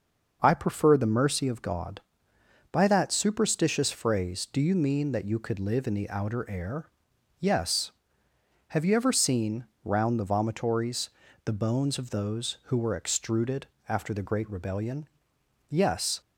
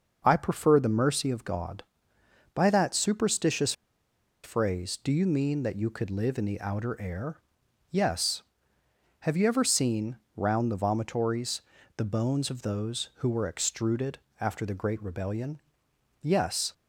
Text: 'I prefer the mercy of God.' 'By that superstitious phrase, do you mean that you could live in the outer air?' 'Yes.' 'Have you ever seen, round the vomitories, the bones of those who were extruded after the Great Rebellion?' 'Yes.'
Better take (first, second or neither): first